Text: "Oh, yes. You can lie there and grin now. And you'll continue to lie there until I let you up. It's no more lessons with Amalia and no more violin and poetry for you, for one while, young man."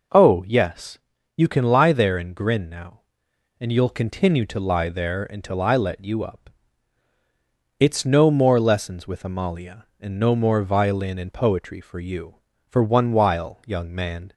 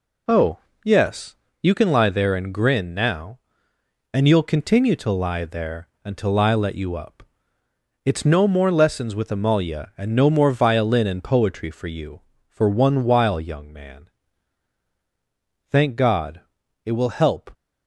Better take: first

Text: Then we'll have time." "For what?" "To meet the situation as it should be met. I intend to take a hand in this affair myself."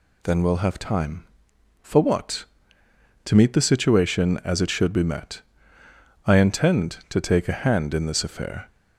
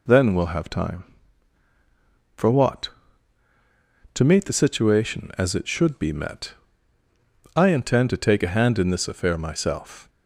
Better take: second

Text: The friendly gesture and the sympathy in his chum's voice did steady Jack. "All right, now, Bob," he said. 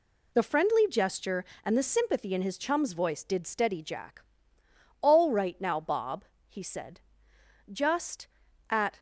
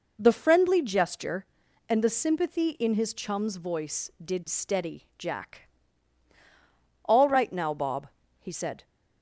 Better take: second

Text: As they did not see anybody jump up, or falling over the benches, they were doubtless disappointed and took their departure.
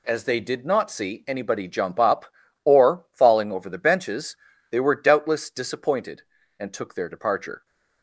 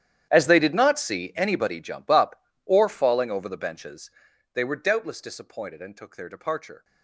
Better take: first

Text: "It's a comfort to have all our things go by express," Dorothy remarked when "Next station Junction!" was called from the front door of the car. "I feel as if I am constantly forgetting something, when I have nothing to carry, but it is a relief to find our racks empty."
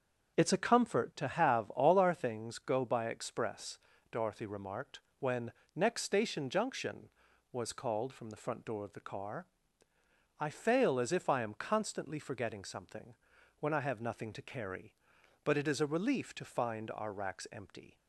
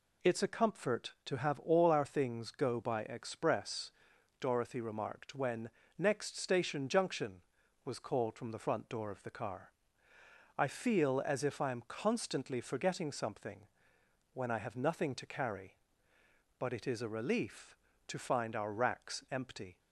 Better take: second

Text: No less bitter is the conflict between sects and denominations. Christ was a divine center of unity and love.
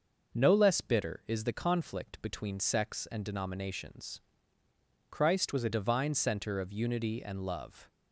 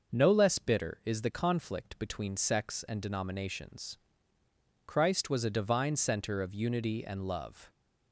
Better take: second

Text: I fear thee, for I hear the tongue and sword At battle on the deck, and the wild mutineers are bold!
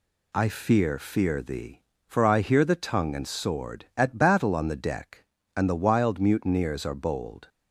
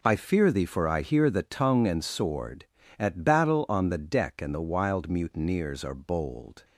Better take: second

